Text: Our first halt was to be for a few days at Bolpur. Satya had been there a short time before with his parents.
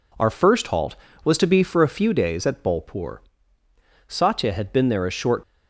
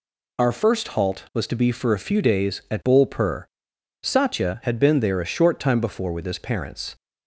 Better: second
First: stops before "time before with his parents"; at 5.4 s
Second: none

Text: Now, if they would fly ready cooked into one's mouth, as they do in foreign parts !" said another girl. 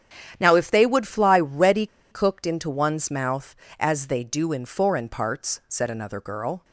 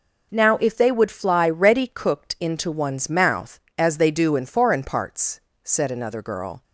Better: second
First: starts louder than the rest; strong; until 1.4 s; 10 dB // pauses between "ready" and "cooked"; slight; at 1.8 s; 0.25 s long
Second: none

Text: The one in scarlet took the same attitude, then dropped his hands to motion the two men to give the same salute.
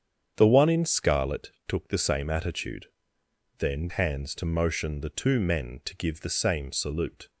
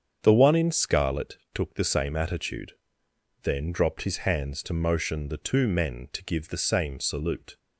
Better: second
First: starts louder than the rest; strong; until 1.3 s; 8 dB // pauses between "scarlet" and "took"; slight; at 1.5 s; 0.16 s long // skips "dropped his"; at 3.8 s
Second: starts louder than the rest; strong; until 1.2 s; 7.5 dB // pauses between "scarlet" and "took"; slight; at 1.3 s; 0.16 s long

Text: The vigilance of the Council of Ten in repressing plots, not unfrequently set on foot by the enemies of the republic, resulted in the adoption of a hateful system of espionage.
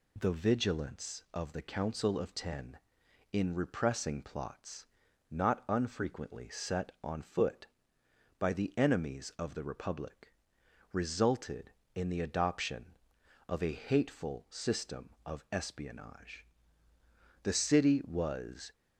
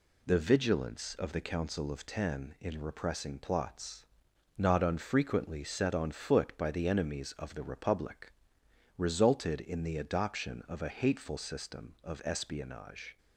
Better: second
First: goes on to say "The city was"; noticeable; from 17.4 s on; 1.3 s long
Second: none

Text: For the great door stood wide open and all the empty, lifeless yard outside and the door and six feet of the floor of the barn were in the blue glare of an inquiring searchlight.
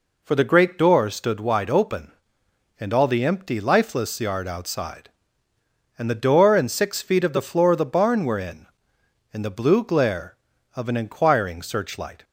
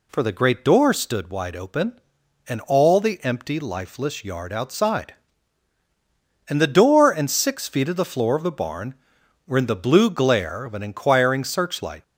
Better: second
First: says "in" twice; at 9.3 s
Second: none

